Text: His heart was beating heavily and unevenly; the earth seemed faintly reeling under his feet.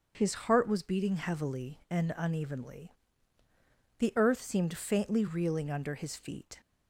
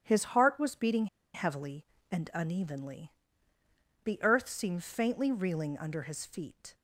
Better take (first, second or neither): first